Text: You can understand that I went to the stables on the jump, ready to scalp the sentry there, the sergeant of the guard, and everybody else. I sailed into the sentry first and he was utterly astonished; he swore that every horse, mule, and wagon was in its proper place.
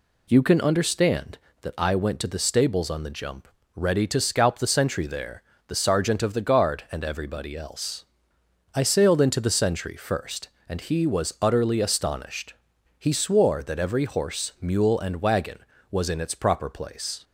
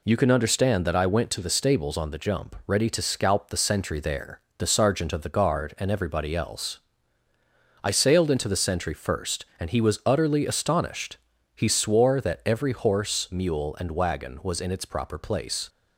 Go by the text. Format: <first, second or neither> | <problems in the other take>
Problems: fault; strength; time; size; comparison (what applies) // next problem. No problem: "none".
neither | none